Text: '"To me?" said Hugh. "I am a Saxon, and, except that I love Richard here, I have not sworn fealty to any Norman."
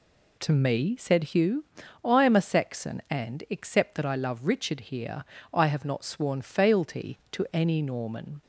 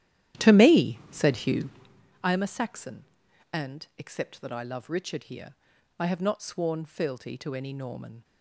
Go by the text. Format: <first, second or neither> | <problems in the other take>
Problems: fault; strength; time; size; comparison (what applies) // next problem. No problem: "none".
first | starts louder than the rest; strong; until 2.1 s; 12 dB